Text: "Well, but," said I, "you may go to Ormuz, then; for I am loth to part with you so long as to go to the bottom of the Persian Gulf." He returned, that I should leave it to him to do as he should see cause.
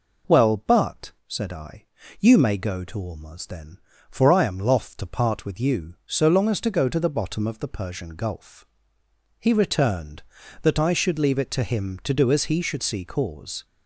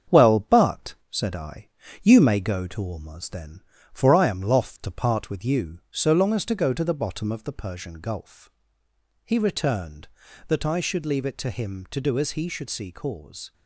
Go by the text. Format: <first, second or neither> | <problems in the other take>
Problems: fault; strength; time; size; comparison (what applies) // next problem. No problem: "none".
first | gets quieter; throughout; 3.5 dB